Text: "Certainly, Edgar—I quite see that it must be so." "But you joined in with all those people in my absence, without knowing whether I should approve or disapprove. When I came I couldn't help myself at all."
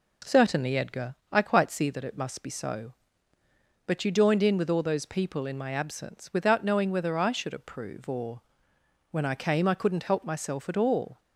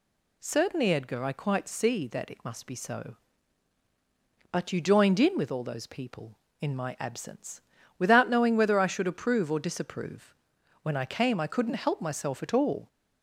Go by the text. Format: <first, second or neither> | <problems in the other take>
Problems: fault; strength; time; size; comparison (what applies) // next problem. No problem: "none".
second | skips "disapprove"; at 8.7 s